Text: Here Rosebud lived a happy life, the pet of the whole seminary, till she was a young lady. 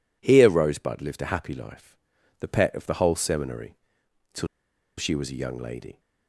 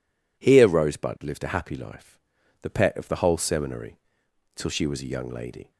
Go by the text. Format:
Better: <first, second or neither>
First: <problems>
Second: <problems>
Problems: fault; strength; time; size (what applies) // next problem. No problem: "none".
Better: second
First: pauses between "till" and "she"; noticeable; at 4.4 s; 0.52 s long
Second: none